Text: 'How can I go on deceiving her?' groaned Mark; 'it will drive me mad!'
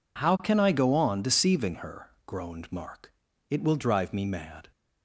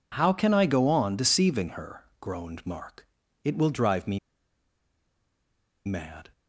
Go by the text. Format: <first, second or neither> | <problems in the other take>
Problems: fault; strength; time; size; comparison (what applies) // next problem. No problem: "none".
first | pauses between "me" and "mad"; strong; at 4.1 s; 1.6 s long